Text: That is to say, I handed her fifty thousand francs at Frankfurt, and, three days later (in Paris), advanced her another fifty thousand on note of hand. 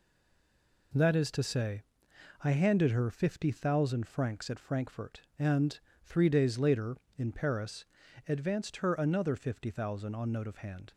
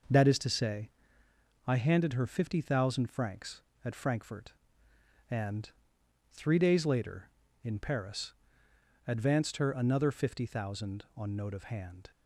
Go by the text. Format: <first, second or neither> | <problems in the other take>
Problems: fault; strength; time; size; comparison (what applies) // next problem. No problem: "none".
second | stays silent before the first word; slight; until 0.9 s; 0.9 s long